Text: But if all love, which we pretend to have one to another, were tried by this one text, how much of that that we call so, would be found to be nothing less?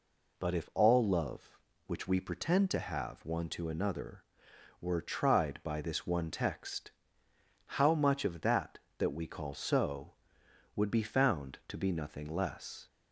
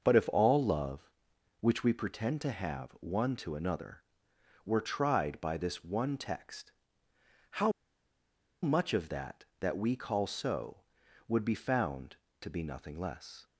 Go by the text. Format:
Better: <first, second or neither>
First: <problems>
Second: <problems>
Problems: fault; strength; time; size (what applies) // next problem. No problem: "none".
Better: first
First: none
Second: starts louder than the rest; until 1.0 s; 6 dB // pauses between "how" and "much"; noticeable; at 7.7 s; 0.91 s long